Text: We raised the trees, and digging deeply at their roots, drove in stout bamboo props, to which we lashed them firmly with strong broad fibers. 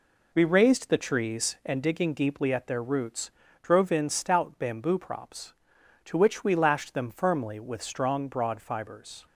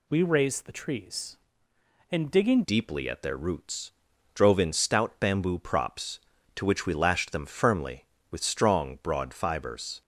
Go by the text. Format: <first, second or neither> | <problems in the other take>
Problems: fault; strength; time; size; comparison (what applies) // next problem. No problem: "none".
first | changes voice at "deeply"; from 2.6 s on; 7.4 s long